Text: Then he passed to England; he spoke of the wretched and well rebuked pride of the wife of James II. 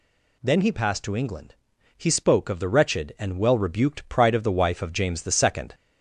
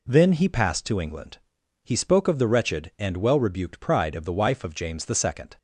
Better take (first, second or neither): second